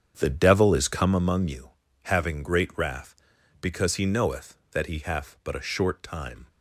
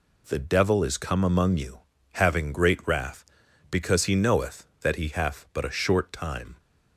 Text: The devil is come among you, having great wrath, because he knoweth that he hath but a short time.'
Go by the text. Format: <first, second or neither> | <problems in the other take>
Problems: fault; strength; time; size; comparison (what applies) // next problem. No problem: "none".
second | starts louder than the rest; strong; until 1.3 s; 8 dB